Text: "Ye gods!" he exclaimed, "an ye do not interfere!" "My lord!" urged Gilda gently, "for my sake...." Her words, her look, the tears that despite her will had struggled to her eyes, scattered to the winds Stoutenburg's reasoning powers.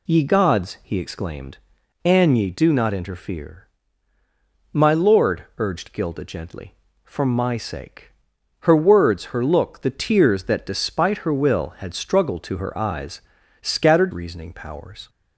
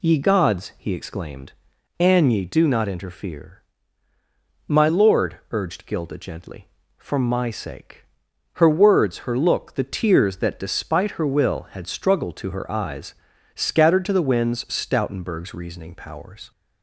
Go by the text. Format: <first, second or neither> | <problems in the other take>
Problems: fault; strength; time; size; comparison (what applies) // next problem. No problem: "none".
second | skips "to the winds Stoutenburg's"; at 14.1 s